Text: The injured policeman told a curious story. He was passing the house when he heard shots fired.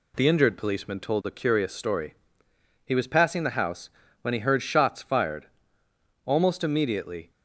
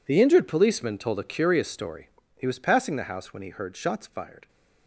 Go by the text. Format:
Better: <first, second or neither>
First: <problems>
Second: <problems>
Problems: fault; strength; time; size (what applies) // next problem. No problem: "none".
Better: second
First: pauses between "house" and "when"; slight; at 3.8 s; 0.32 s long // goes on to say "Almost immediately"; noticeable; from 6.2 s on; 1.0 s long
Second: none